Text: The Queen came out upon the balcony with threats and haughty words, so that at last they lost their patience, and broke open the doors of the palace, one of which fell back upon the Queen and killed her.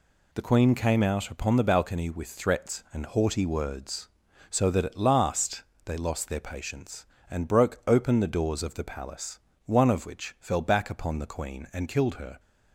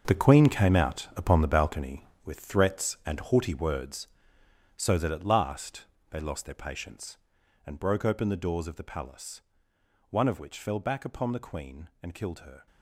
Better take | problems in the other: first | gets quieter; strong; throughout; 13 dB // pauses between "last" and "they"; slight; at 5.8 s; 0.24 s long; slight in the first

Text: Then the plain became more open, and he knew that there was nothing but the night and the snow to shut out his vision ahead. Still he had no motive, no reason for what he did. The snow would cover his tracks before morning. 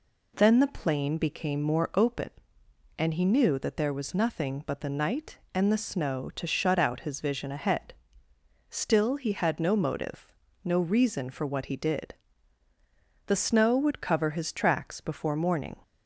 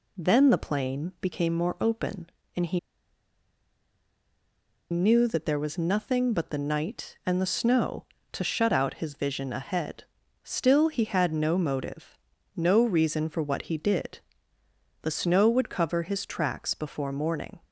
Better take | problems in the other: first | pauses between "he" and "knew"; strong; at 2.7 s; 2.1 s long

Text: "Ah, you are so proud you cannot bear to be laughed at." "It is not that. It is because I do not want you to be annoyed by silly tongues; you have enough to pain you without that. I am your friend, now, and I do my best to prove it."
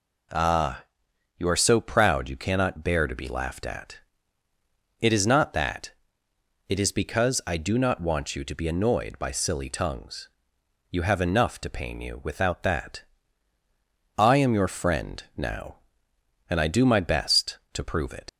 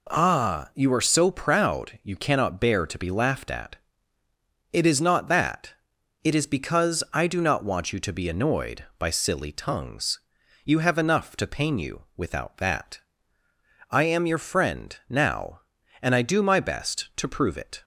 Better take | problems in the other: second | leaves "it" unfinished; at 18.2 s; 75 ms

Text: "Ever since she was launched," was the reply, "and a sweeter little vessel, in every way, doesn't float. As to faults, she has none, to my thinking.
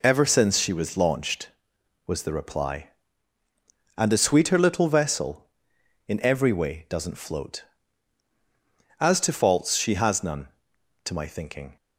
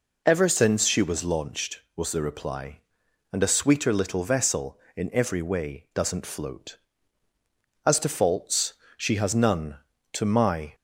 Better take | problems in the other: first | stops before "thinking"; at 10.7 s

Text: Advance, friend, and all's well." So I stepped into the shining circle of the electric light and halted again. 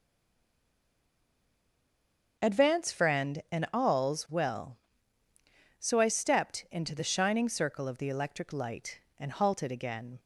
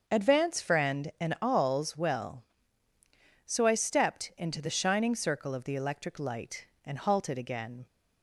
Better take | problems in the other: second | stays silent before the first word; until 2.3 s; 2.3 s long // starts louder than the rest; until 3.4 s; 6 dB; also in the second

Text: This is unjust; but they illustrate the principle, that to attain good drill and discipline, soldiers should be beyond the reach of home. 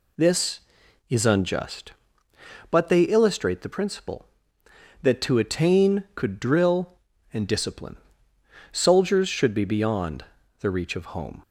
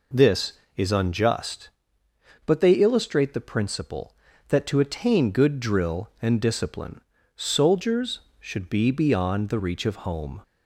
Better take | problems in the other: second | says "could" for "good"; at 6.1 s // pauses between "beyond" and "the"; slight; at 10.2 s; 0.36 s long

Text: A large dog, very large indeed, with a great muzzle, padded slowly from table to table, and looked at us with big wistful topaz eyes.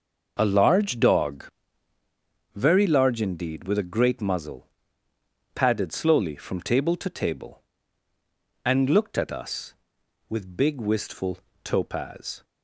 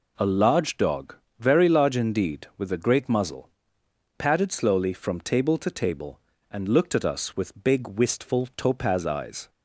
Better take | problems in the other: second | pauses between "wistful" and "topaz"; slight; at 11.3 s; 0.26 s long // stops before "eyes"; at 12.4 s

